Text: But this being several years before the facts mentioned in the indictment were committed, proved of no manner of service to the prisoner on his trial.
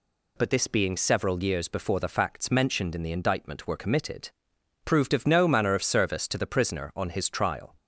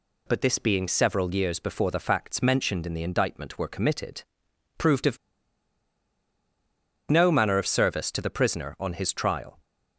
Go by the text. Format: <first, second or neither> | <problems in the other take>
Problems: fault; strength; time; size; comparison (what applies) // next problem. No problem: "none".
first | pauses between "of" and "no"; strong; at 5.1 s; 1.9 s long